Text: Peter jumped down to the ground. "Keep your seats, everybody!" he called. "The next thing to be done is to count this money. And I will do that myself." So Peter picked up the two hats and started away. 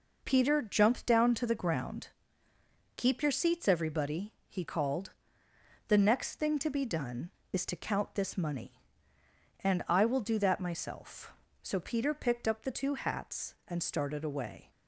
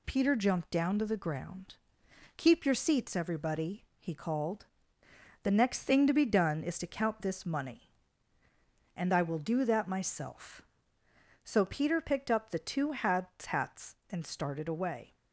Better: first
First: none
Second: says "hats" twice; at 13.4 s

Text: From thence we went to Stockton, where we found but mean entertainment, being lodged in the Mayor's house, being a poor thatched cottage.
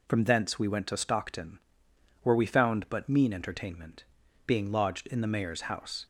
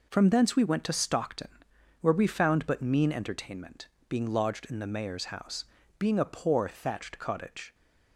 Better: second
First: stops before "being a poor thatched cottage"; at 6.0 s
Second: none

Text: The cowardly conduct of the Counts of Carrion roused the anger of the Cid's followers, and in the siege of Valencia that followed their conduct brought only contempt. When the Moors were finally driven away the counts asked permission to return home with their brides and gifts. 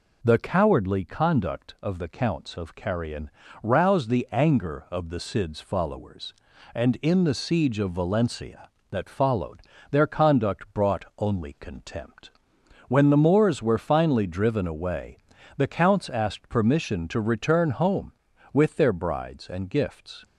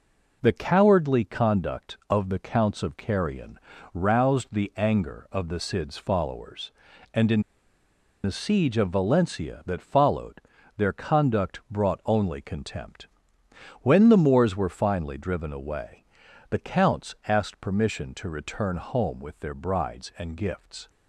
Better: first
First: pauses between "Carrion" and "roused"; slight; at 3.2 s; 0.32 s long // pauses between "followed" and "their"; slight; at 9.6 s; 0.28 s long // pauses between "away" and "the"; at 15.1 s; 0.38 s long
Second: pauses between "Carrion" and "roused"; slight; at 3.5 s; 0.34 s long // pauses between "in" and "the"; noticeable; at 7.3 s; 0.84 s long // pauses between "followed" and "their"; at 10.3 s; 0.38 s long // pauses between "away" and "the"; noticeable; at 16.0 s; 0.46 s long

